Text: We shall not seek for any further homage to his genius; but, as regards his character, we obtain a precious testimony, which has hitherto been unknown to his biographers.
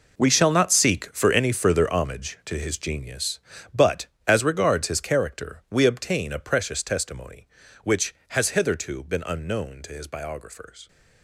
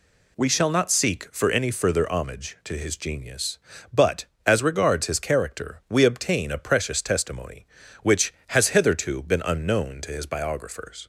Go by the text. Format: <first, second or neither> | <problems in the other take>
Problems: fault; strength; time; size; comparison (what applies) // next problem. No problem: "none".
second | gets quieter; strong; throughout; 13.5 dB